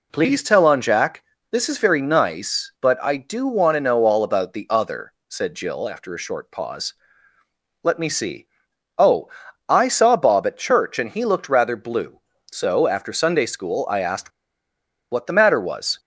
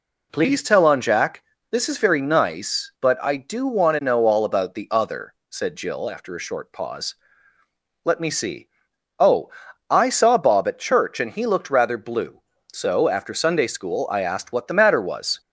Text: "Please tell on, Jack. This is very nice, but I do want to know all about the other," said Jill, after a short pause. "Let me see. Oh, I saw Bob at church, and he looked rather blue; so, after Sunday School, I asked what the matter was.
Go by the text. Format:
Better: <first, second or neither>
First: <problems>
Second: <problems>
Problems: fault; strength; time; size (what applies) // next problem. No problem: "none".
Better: second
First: pauses between "asked" and "what"; noticeable; at 14.3 s; 0.80 s long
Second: none